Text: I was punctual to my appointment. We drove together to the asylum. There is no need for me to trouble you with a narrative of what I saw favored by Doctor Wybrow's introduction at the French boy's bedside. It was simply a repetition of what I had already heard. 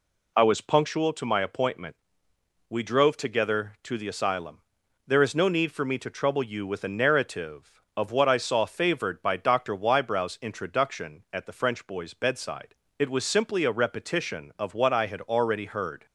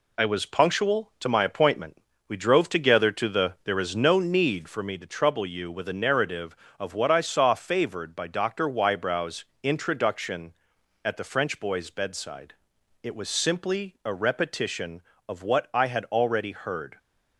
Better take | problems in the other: first | skips "asylum"; at 3.5 s // pauses between "Wybrow's" and "introduction"; slight; at 9.4 s; 0.16 s long

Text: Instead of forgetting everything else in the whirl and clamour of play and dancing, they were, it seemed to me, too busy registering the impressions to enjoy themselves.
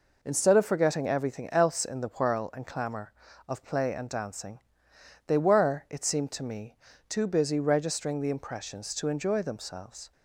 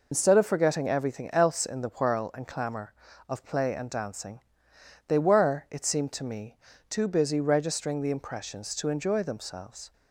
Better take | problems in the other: first | loses the start of "Instead"; at 0.1 s; 75 ms

